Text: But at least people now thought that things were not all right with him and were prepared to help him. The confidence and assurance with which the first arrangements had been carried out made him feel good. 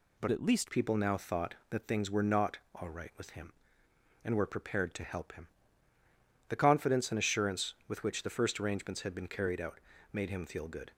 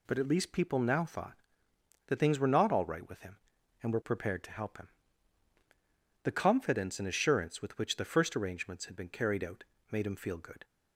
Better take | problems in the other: second | changes voice from "at" to "least"; from 0.3 to 0.7 s; 0.4 s long // pauses between "not" and "all"; slight; at 2.5 s; 0.16 s long // pauses between "out" and "made"; slight; at 9.7 s; 0.34 s long; slight in the second

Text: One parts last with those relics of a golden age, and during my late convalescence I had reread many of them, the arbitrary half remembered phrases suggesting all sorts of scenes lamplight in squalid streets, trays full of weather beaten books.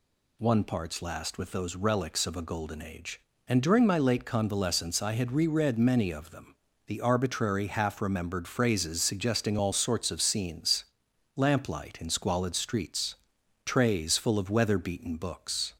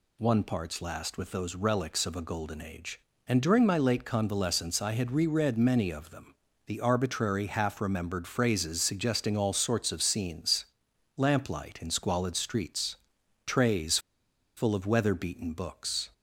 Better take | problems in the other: first | pauses between "scenes" and "lamplight"; noticeable; at 10.6 s; 0.50 s long; noticeable in the first // pauses between "trays" and "full"; noticeable; at 13.9 s; 0.58 s long

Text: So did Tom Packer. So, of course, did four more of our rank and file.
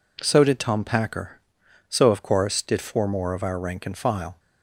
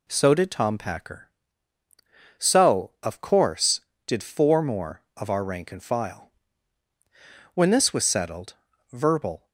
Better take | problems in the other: first | goes on to say "When this was settled verbal"; strong; from 7.5 s on; 1.9 s long

